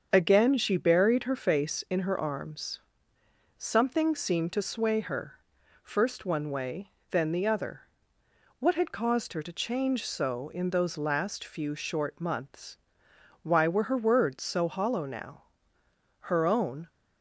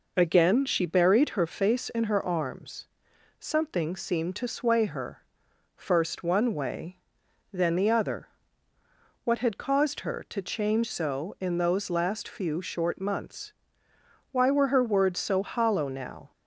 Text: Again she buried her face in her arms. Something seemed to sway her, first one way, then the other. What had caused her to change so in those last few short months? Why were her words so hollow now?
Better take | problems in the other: second | starts louder than the rest; until 1.1 s; 7 dB // goes on to say "Her own"; noticeable; from 16.2 s on; 0.64 s long

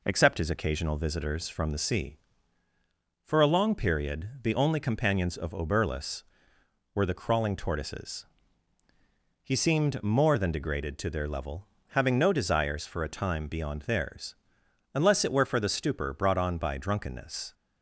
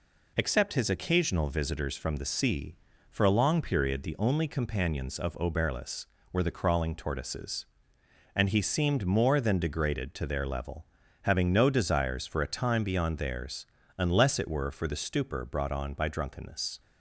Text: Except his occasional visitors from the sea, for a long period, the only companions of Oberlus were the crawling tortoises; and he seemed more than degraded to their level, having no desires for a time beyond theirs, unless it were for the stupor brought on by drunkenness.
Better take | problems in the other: second | skips "and"; at 8.8 s

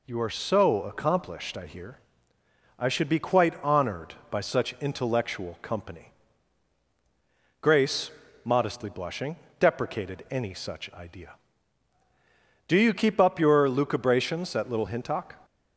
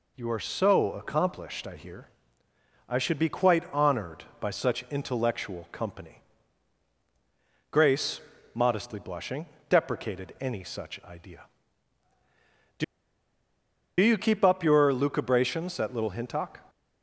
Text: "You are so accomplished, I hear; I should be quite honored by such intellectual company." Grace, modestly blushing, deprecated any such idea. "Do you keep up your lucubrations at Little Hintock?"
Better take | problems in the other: first | pauses between "Do" and "you"; at 12.8 s; 1.1 s long

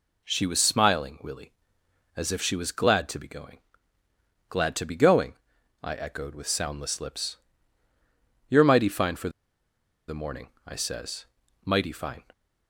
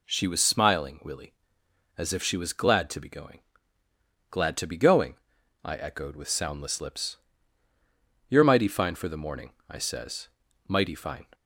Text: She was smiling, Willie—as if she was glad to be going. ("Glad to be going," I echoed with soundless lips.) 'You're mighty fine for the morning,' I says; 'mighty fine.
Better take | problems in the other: second | pauses between "for" and "the"; noticeable; at 9.2 s; 0.79 s long

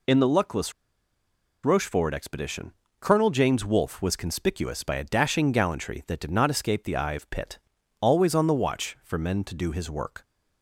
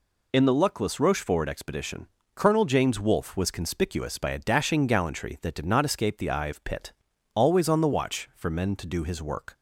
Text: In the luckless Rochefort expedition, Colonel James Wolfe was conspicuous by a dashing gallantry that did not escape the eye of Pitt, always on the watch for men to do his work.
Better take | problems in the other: second | pauses between "luckless" and "Rochefort"; noticeable; at 0.7 s; 0.92 s long

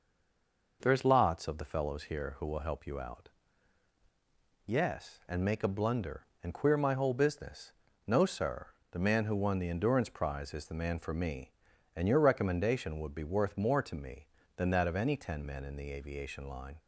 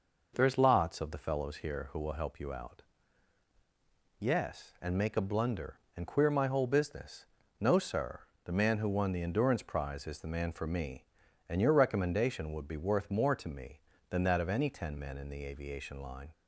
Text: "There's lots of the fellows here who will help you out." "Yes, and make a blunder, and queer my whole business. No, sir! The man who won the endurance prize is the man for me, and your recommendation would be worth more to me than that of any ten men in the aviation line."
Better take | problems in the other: second | stays silent before the first word; slight; until 0.8 s; 0.8 s long

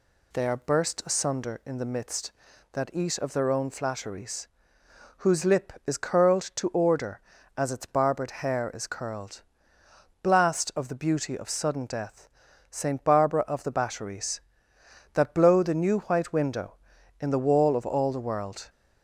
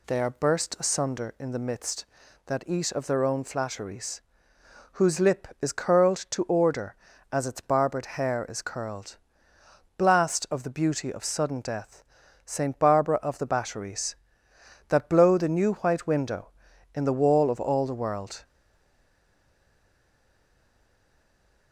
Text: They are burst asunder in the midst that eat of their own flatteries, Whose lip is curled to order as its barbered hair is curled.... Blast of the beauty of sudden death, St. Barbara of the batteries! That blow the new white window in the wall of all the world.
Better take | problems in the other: first | stays silent after the last word; strong; from 18.4 s on; 3.3 s long

